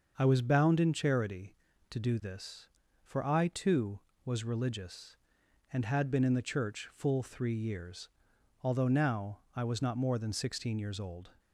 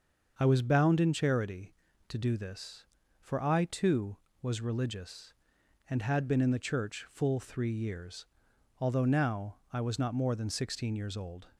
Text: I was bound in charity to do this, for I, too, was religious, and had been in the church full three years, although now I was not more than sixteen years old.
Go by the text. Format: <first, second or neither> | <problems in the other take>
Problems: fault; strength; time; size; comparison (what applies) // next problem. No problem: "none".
neither | starts louder than the rest; the same in both